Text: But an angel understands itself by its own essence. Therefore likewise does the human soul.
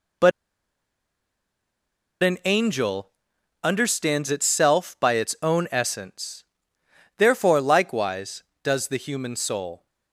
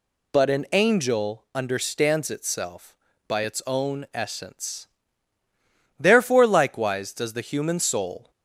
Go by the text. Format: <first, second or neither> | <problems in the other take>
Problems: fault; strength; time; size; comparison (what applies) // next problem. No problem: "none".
second | pauses between "But" and "an"; strong; at 0.3 s; 1.9 s long // pauses between "angel" and "understands"; noticeable; at 3.0 s; 0.54 s long